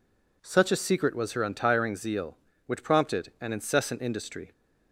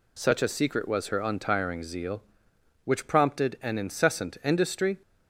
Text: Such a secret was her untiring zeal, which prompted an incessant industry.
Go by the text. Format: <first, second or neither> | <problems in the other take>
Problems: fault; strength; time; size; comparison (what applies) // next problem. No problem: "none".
neither | none